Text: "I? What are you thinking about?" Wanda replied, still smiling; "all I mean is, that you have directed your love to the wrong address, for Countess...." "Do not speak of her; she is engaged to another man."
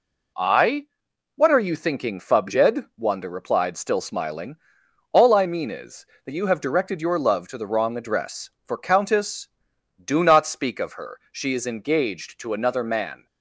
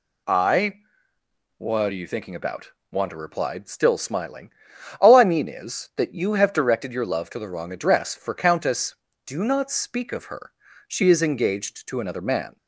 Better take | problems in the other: second | says "fubjed" for "about"; at 2.1 s

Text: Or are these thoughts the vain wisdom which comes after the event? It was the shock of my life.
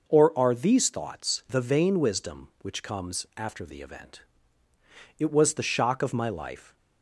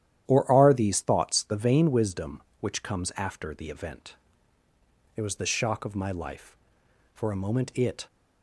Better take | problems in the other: first | starts louder than the rest; strong; until 1.2 s; 11 dB // goes on to say "For a moment it"; noticeable; from 7.1 s on; 0.92 s long

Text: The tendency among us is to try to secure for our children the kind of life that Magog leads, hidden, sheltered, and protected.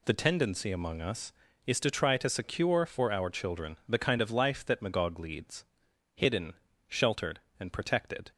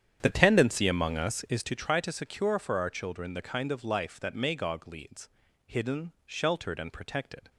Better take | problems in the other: first | starts louder than the rest; strong; until 1.7 s; 9.5 dB

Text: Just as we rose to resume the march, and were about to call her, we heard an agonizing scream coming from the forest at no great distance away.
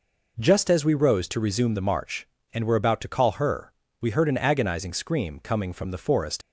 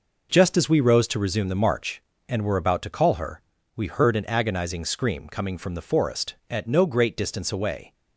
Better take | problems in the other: second | stops before "at no great distance away"; at 6.4 s

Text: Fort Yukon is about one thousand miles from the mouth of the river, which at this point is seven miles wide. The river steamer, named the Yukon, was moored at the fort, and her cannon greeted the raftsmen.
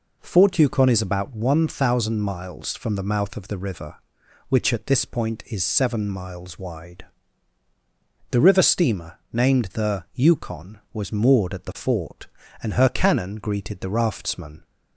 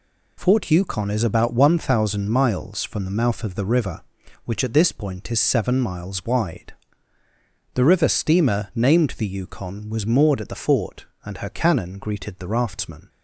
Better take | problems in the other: neither | none

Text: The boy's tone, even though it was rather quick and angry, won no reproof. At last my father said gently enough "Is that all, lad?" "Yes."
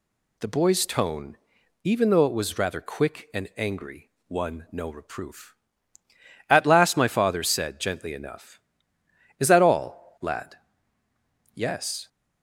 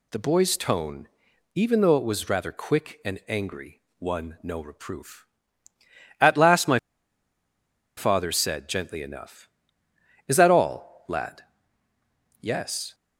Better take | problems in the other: first | pauses between "my" and "father"; at 6.7 s; 1.1 s long

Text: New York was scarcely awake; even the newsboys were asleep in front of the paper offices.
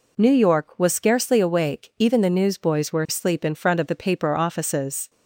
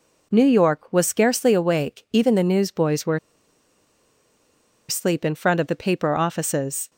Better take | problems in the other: first | pauses between "were" and "asleep"; strong; at 3.1 s; 1.7 s long

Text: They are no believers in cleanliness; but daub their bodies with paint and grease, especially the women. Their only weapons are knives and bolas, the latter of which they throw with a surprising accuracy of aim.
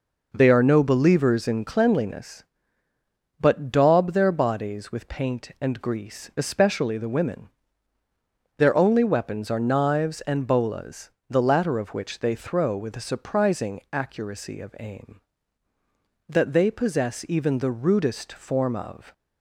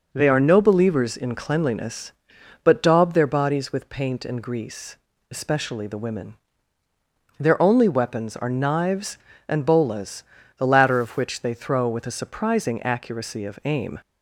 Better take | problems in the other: second | goes on to say "That they possess even the rudest form of"; strong; from 16.2 s on; 2.8 s long

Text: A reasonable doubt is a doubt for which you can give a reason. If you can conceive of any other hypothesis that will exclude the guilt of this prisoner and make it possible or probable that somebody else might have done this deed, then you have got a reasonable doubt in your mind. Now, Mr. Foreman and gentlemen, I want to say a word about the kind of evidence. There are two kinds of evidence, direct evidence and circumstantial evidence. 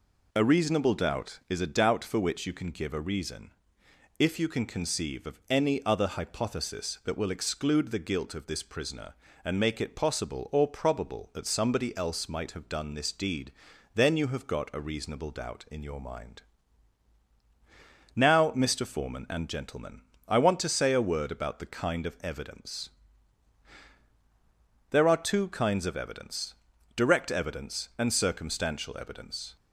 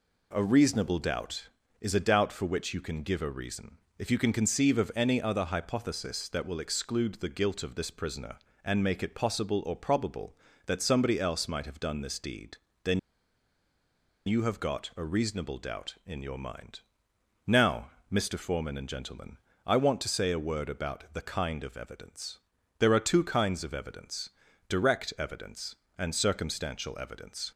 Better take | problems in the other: first | pauses between "then" and "you"; strong; at 12.9 s; 1.2 s long

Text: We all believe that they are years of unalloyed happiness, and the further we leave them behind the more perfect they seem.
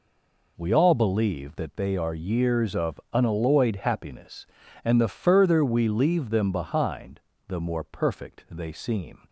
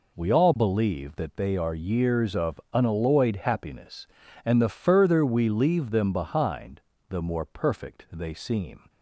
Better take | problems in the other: second | stays silent before the first word; slight; until 0.5 s; 0.5 s long // pauses between "behind" and "the"; slight; at 7.2 s; 0.27 s long; slight in the second

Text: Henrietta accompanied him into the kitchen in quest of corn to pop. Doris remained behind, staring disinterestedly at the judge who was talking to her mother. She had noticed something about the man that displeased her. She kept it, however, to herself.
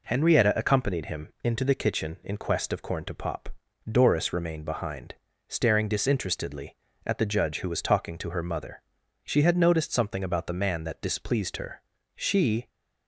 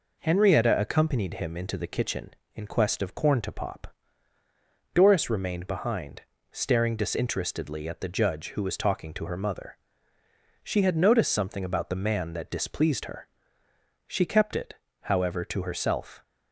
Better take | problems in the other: second | stops before "kept it however to herself"; at 12.6 s

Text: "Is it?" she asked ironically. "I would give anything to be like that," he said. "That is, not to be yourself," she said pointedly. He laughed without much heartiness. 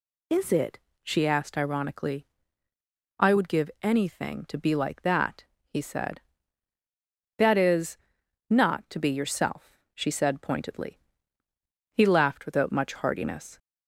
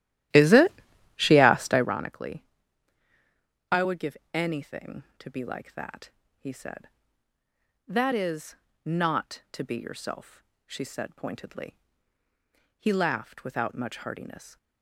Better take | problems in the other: first | starts louder than the rest; strong; until 2.0 s; 13 dB // pauses between "give" and "anything"; slight; at 4.1 s; 0.16 s long

